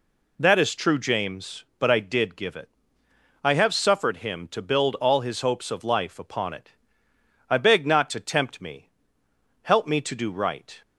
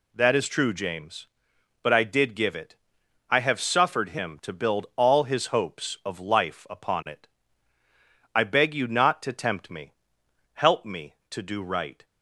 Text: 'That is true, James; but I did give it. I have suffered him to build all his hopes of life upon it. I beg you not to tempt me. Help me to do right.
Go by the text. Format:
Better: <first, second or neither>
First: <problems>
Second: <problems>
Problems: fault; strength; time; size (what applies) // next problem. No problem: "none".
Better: second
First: skips "you"; at 7.8 s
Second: none